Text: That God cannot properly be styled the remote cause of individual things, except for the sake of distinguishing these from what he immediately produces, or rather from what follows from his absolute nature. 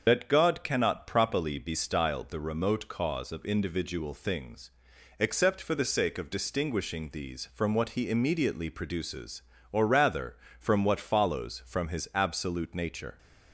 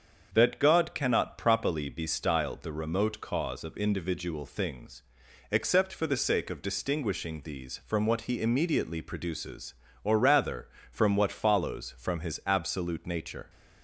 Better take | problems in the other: second | loses the start of "That"; at 0.0 s; 55 ms // starts louder than the rest; until 1.0 s; 6.5 dB; also in the second

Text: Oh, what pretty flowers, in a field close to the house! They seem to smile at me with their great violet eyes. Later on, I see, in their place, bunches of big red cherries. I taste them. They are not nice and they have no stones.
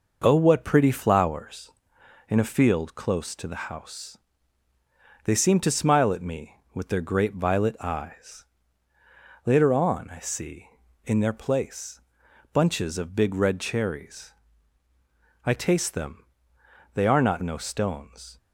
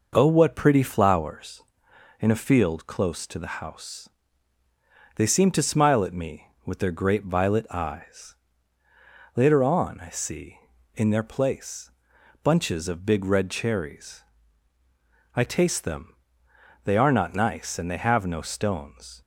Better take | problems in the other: second | skips "nice and they have"; at 17.4 s

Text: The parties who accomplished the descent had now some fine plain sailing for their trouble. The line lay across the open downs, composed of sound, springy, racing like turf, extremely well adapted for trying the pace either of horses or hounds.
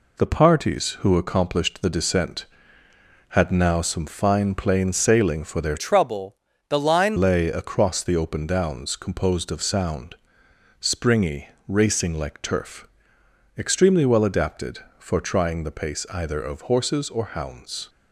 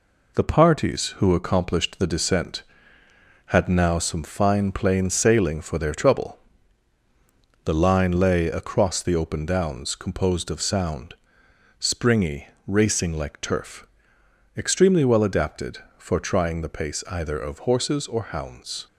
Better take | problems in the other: second | changes voice from "trouble" to "line"; from 5.7 to 7.1 s; 1.4 s long

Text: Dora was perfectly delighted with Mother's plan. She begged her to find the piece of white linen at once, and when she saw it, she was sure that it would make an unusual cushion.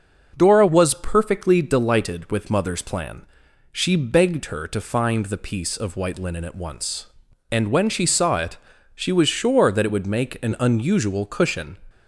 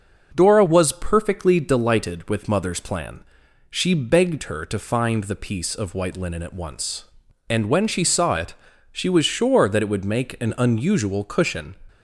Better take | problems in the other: neither | starts louder than the rest; the same in both

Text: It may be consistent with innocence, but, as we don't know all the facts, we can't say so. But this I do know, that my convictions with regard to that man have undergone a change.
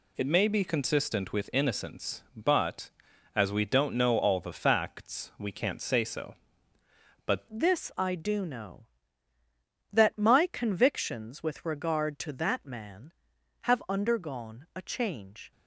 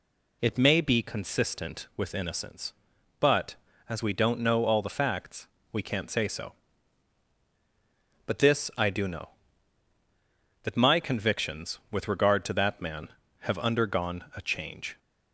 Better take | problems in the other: second | changes voice at "this"; from 7.5 s on; 8.0 s long

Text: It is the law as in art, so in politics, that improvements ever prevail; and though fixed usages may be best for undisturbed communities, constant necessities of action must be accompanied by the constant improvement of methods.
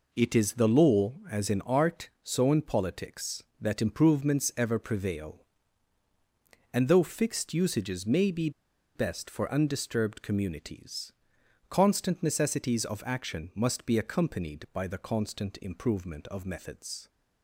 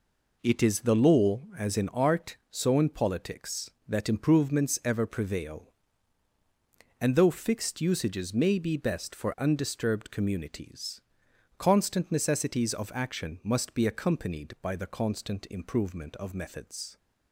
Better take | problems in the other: second | pauses between "be" and "best"; at 8.4 s; 0.45 s long

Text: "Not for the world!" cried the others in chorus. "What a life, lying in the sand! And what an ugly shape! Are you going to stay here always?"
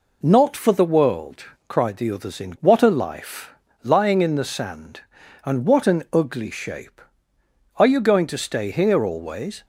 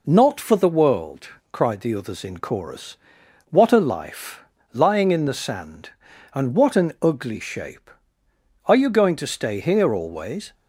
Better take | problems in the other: second | skips "chorus"; at 2.5 s

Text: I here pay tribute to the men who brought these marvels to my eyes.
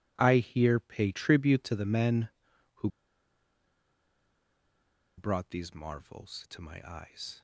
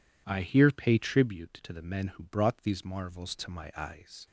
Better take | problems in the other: second | pauses between "who" and "brought"; strong; at 2.8 s; 2.3 s long

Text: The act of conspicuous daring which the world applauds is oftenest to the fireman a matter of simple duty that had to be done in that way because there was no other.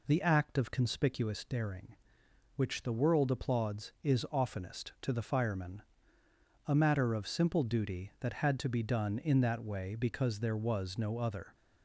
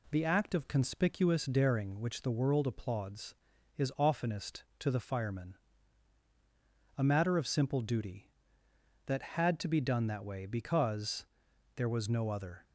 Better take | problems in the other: first | pauses between "fireman" and "a"; strong; at 5.5 s; 1.4 s long; noticeable in the first // skips "in"; at 10.0 s // pauses between "because" and "there"; noticeable; at 11.2 s; 0.48 s long

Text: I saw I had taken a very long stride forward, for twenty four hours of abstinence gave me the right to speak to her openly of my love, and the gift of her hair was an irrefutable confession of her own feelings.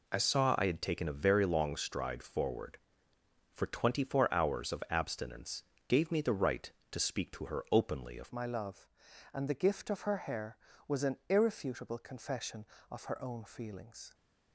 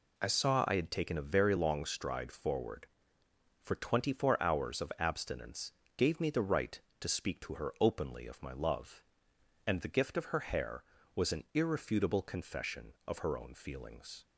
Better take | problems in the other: second | pauses between "abstinence" and "gave"; slight; at 5.6 s; 0.26 s long; slight in the second // changes voice at "my"; from 8.2 s on; 5.9 s long

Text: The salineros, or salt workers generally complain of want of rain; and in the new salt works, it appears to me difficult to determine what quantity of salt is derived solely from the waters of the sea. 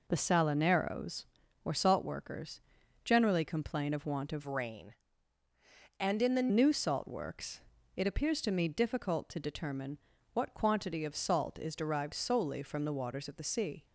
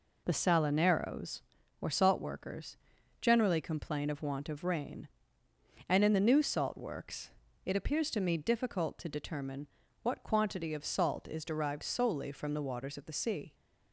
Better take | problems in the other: second | pauses between "workers" and "generally"; at 2.6 s; 0.42 s long; also in the second // changes voice from "rain" to "the"; from 4.4 to 6.4 s; 2.0 s long // pauses between "determine" and "what"; slight; at 9.9 s; 0.36 s long; slight in the second

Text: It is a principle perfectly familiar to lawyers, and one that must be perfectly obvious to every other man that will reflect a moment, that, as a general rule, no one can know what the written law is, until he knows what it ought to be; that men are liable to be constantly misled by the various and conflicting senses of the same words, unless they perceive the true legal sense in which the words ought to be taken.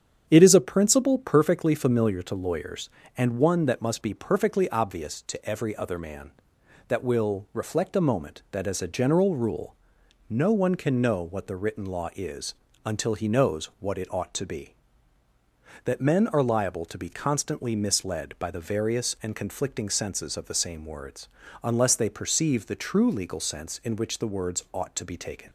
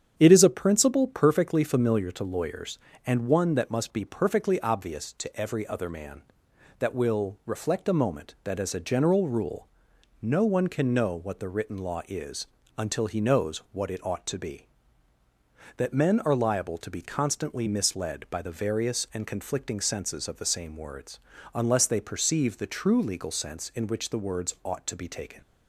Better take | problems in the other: neither | starts louder than the rest; strong; the same in both

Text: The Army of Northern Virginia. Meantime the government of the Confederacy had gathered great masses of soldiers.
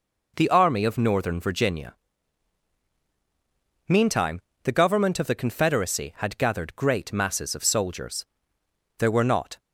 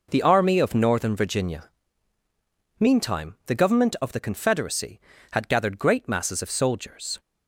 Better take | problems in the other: second | pauses between "Meantime" and "the"; slight; at 4.4 s; 0.22 s long // goes on to say "There were not"; noticeable; from 8.9 s on; 0.62 s long

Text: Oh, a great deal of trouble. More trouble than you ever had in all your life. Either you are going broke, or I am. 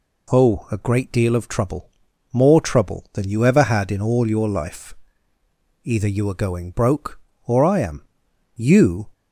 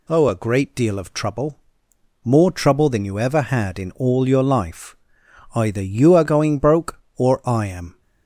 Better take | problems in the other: second | goes on to say "You"; from 8.5 s on; 0.54 s long

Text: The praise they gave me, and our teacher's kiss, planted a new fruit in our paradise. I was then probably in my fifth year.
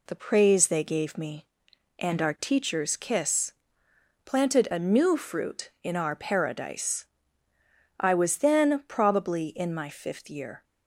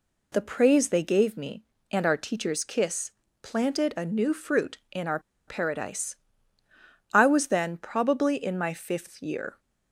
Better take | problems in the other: first | pauses between "our" and "paradise"; slight; at 5.1 s; 0.28 s long

